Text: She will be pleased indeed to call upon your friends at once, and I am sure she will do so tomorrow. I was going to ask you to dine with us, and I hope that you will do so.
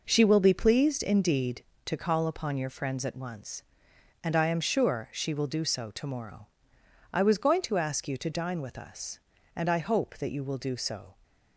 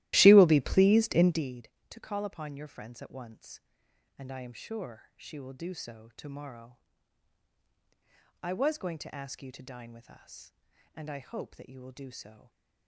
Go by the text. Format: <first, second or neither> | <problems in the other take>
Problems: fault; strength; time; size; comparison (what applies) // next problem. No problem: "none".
first | starts louder than the rest; strong; until 1.5 s; 16 dB // stays silent after the last word; slight; from 12.3 s on; 0.5 s long